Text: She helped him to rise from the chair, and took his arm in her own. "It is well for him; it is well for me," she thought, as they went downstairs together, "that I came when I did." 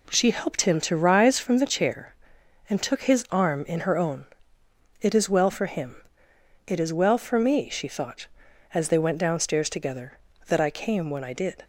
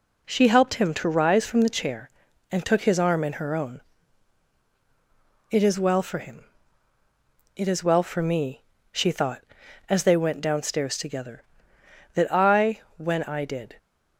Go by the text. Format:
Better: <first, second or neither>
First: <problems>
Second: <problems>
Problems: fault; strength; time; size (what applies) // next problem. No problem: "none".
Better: first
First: none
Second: skips "came"; at 12.8 s